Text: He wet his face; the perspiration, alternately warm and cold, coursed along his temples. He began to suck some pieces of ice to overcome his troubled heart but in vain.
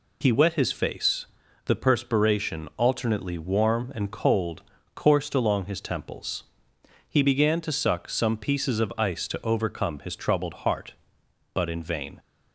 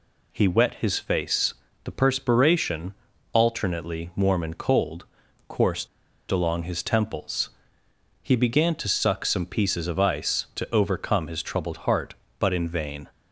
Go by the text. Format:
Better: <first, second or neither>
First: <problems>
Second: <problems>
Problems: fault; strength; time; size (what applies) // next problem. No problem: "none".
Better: first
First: none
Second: pauses between "coursed" and "along"; at 5.8 s; 0.43 s long